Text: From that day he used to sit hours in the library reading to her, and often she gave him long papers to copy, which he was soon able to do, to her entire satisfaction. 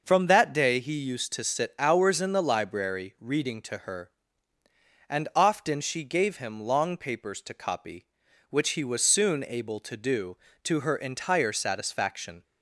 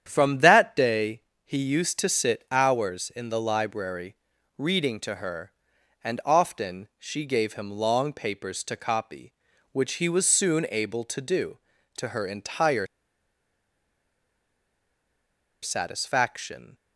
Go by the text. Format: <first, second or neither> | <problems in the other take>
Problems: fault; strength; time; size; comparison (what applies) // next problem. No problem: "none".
first | starts louder than the rest; strong; until 1.1 s; 9 dB; noticeable in the first // pauses between "day" and "he"; slight; at 1.2 s; 0.22 s long // pauses between "library" and "reading"; at 4.1 s; 0.42 s long // pauses between "entire" and "satisfaction"; strong; at 12.8 s; 2.7 s long